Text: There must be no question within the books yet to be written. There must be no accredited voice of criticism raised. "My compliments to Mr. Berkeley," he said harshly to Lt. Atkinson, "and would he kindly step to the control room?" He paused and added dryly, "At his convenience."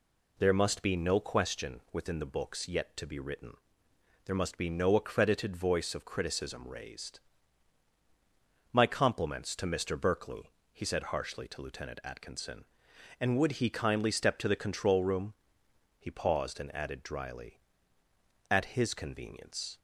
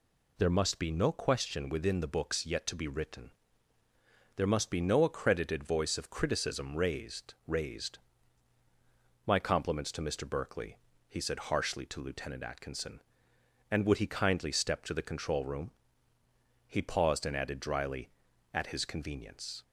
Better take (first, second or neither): first